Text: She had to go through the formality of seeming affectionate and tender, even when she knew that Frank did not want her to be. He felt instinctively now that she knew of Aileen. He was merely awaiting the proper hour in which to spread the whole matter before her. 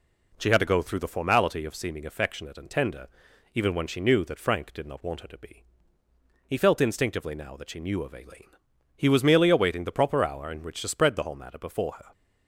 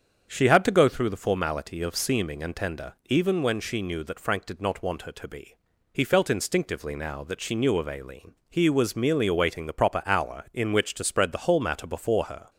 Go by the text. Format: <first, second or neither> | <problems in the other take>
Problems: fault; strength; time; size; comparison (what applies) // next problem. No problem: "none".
first | starts louder than the rest; strong; until 1.3 s; 7.5 dB // skips "affectionate"; at 2.4 s